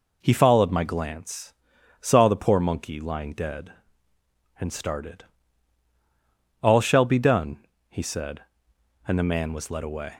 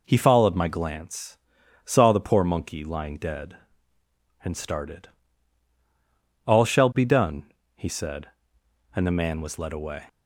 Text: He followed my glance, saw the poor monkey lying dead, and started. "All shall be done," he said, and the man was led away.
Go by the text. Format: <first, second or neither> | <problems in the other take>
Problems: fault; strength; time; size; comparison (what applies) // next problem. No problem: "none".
neither | none